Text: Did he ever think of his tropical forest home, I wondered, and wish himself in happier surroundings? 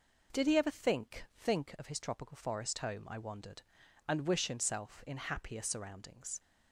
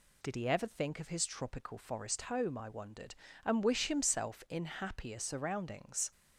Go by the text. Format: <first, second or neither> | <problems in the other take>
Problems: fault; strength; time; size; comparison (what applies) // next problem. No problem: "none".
second | says "think" twice; at 1.3 s